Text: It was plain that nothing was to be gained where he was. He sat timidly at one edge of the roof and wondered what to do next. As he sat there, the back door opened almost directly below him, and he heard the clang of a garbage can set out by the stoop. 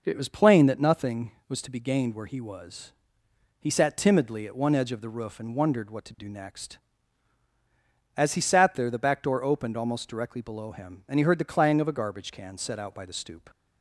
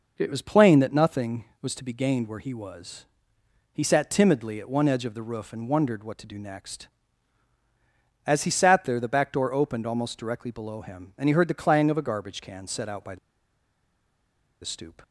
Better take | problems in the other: first | pauses between "the" and "stoop"; strong; at 13.1 s; 1.4 s long

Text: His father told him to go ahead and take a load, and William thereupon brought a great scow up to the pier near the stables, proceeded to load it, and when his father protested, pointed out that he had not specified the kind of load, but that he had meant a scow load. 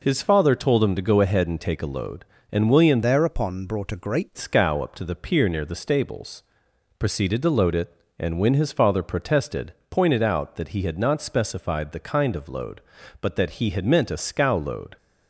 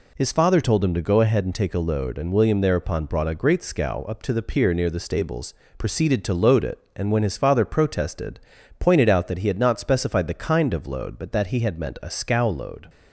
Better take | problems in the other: second | changes voice from "thereupon" to "great"; from 3.0 to 4.3 s; 1.3 s long

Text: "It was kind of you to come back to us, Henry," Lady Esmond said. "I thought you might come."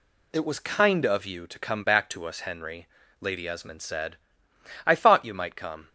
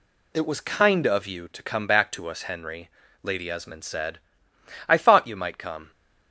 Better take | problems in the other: neither | none

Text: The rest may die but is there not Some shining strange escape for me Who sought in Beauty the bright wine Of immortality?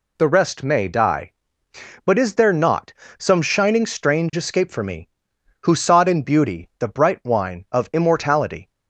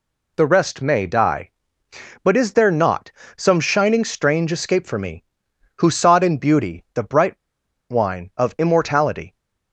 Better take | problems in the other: first | pauses between "not" and "Some"; slight; at 3.1 s; 0.24 s long; slight in the first // pauses between "bright" and "wine"; noticeable; at 7.3 s; 0.50 s long

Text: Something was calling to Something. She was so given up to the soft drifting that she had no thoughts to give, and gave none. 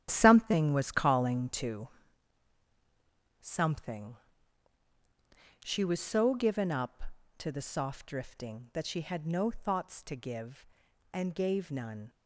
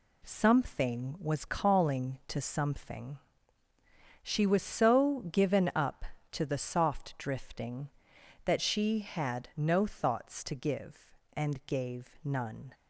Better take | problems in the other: second | gets quieter; strong; throughout; 10.5 dB // pauses between "to" and "Something"; strong; at 1.8 s; 1.5 s long

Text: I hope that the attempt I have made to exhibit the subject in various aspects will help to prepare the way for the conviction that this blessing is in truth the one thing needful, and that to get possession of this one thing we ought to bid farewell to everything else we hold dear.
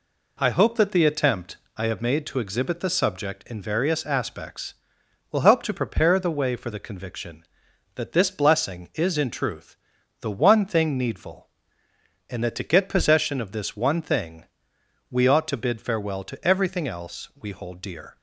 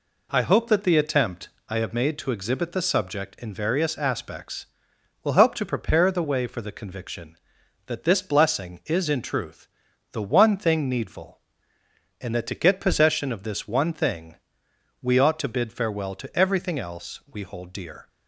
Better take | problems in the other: neither | pauses between "attempt" and "I"; slight; the same in both // pauses between "truth" and "the"; the same in both // pauses between "thing" and "we"; noticeable; the same in both

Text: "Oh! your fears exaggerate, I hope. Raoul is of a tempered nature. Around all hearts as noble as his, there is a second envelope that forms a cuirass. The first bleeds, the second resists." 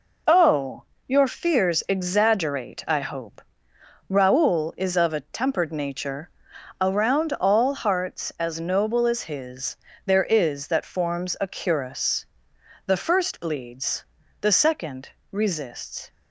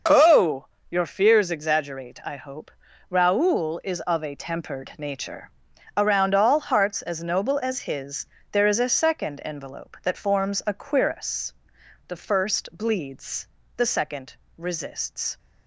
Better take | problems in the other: second | skips "a second envelope"; at 10.6 s // pauses between "second" and "resists"; slight; at 15.0 s; 0.20 s long; slight in the second

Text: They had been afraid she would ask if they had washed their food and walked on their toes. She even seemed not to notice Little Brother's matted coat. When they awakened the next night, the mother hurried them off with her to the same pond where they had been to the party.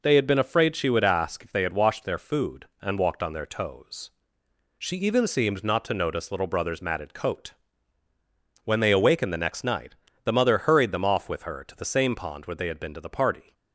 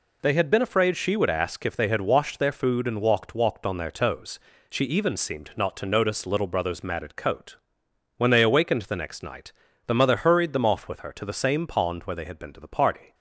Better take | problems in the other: first | says "walked" twice; at 3.3 s

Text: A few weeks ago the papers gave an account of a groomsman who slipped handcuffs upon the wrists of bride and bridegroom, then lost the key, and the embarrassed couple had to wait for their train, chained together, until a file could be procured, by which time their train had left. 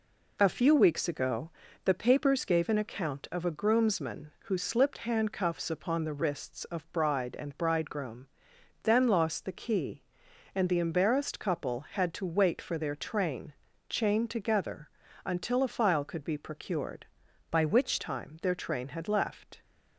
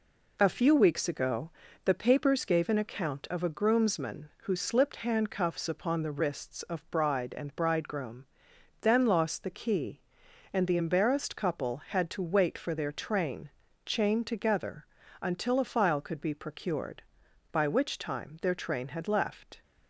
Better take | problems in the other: second | pauses between "ago" and "the"; slight; at 1.5 s; 0.32 s long; slight in the second // changes voice from "by" to "which"; from 17.5 to 18.0 s; 0.5 s long

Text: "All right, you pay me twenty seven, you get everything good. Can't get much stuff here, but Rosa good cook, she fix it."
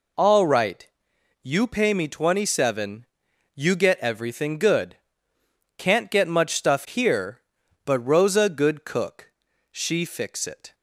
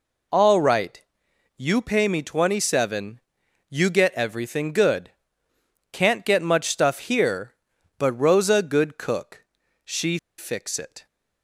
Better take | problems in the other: first | pauses between "she" and "fix"; slight; at 10.1 s; 0.20 s long

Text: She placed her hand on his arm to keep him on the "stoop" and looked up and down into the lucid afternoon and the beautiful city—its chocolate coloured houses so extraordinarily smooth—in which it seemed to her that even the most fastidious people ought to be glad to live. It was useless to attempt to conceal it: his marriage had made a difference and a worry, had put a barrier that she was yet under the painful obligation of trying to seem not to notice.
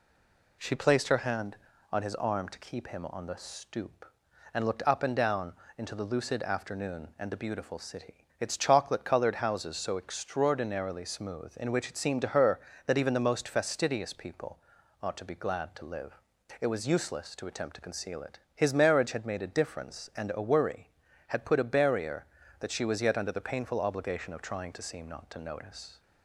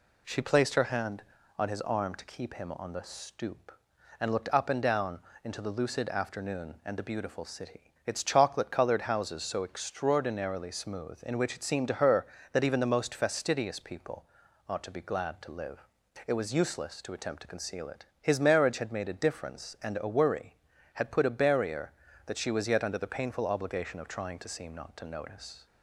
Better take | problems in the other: second | stays silent before the first word; slight; until 0.5 s; 0.5 s long // pauses between "down" and "into"; slight; at 5.5 s; 0.24 s long; slight in the second // pauses between "people" and "ought"; at 14.5 s; 0.42 s long; also in the second

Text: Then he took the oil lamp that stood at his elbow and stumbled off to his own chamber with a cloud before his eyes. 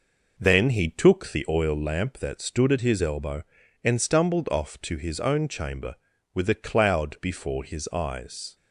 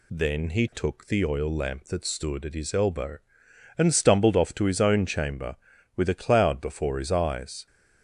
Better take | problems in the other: second | starts louder than the rest; noticeable; until 1.7 s; 5 dB

